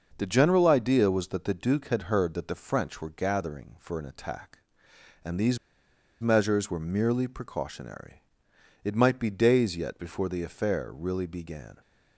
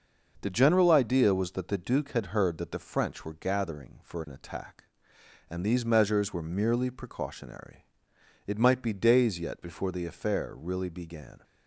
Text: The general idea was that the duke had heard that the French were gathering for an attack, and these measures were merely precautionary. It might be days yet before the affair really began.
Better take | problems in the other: second | pauses between "these" and "measures"; noticeable; at 5.5 s; 0.63 s long

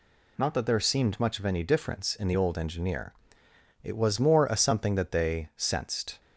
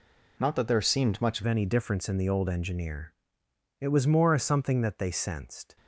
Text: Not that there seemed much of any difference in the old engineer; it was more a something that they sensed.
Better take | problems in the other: first | changes voice at "any"; from 1.4 s on; 4.3 s long

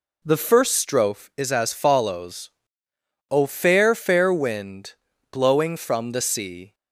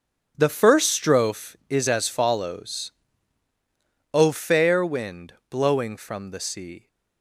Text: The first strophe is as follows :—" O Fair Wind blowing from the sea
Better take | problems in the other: second | says "Fair" twice; at 3.9 s // pauses between "Wind" and "blowing"; at 4.9 s; 0.38 s long; slight in the second

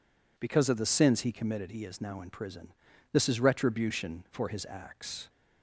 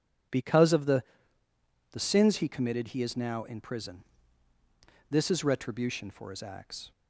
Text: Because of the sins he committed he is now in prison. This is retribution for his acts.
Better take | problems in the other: first | says "the" twice; at 1.9 s

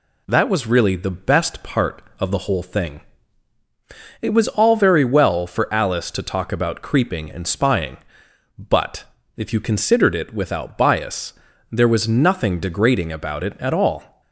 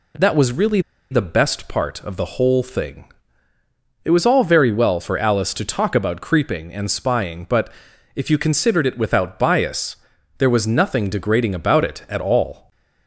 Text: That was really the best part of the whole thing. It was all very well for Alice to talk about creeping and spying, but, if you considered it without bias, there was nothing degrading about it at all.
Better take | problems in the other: first | pauses between "really" and "the"; slight; at 0.7 s; 0.31 s long

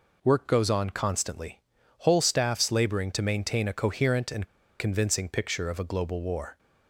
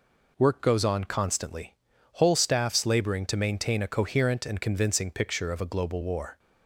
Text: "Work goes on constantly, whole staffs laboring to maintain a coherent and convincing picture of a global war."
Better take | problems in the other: second | pauses between "and" and "convincing"; slight; at 4.4 s; 0.33 s long

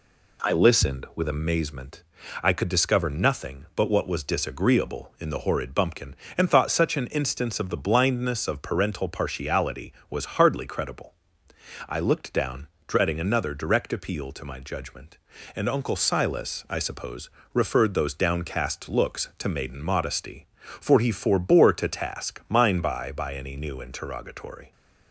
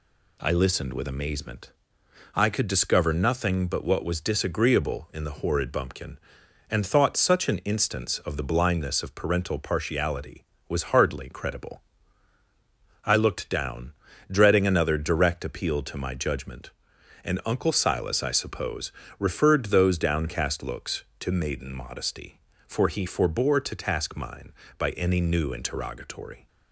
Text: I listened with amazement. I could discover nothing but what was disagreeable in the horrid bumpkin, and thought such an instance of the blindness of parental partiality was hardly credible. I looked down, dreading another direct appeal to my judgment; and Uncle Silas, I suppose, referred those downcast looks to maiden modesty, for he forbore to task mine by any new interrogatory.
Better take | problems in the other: second | says "by" twice; at 23.1 s

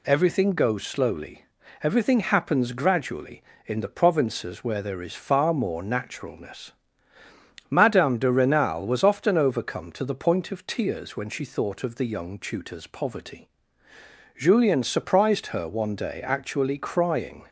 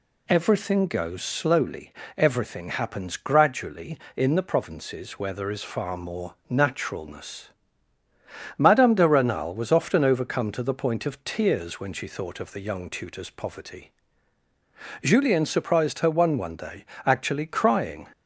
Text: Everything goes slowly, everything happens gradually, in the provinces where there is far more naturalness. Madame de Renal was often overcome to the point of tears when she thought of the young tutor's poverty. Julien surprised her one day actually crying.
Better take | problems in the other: first | says "one" twice; at 16.3 s // pauses between "day" and "actually"; slight; at 16.8 s; 0.20 s long

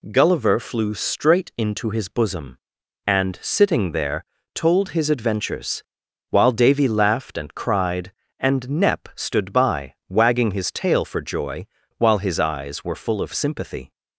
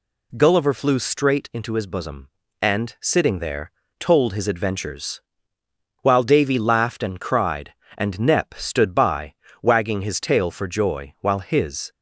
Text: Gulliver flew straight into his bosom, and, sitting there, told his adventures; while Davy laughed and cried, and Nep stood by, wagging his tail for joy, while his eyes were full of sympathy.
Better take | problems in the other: first | stops before "eyes were full of sympathy"; at 11.9 s

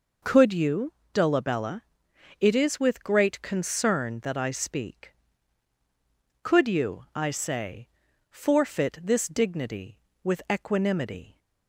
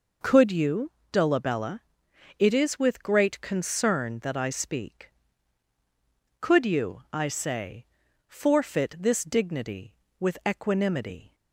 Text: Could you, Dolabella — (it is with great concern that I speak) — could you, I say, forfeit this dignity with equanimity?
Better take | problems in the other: neither | none

